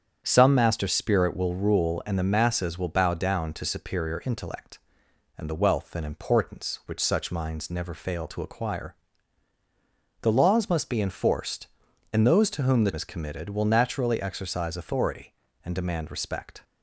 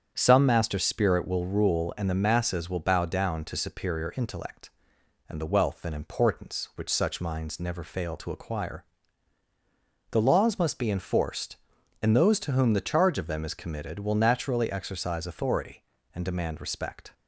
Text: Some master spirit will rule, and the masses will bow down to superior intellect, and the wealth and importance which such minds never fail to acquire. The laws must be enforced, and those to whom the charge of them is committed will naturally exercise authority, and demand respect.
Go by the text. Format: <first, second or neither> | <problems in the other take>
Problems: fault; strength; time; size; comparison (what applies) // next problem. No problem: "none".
second | starts louder than the rest; strong; until 1.2 s; 8 dB; strong in the second // skips "charge of them"; at 12.9 s